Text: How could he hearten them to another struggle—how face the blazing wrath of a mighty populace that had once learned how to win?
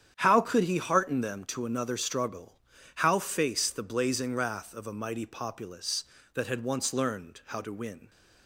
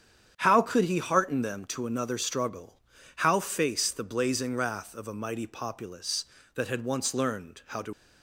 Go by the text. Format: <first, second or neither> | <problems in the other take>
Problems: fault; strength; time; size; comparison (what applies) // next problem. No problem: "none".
first | starts louder than the rest; strong; until 1.3 s; 8.5 dB; strong in the first // stops before "win"; at 7.9 s